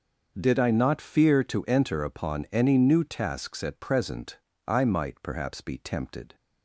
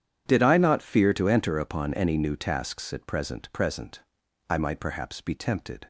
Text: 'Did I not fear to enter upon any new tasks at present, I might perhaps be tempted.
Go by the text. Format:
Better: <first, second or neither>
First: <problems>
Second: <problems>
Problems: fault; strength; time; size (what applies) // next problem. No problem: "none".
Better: first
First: starts louder than the rest; noticeable; until 1.3 s; 6 dB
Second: starts louder than the rest; strong; until 1.2 s; 9 dB // says "present" twice; at 3.5 s